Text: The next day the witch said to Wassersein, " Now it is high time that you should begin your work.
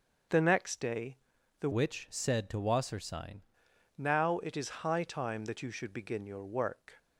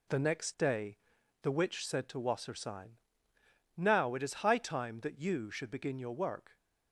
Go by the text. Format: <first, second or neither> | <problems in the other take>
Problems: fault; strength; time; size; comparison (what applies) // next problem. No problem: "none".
second | pauses between "day" and "the"; at 1.1 s; 0.42 s long; noticeable in the second // changes voice from "witch" to "Wassersein"; from 1.7 to 3.4 s; 1.7 s long